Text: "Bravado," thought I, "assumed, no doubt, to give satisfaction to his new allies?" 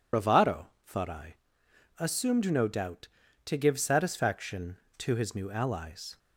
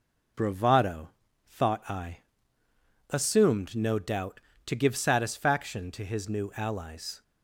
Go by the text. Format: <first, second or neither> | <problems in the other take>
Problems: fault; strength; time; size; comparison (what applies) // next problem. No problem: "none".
second | loses the start of "Bravado"; at 0.1 s; 75 ms